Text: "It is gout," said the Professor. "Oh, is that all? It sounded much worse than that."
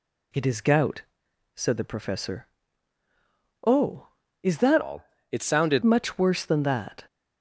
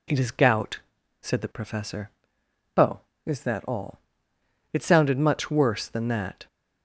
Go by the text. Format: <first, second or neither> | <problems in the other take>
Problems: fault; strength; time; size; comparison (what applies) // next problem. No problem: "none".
second | changes voice from "all" to "sounded"; from 4.8 to 5.8 s; 1.0 s long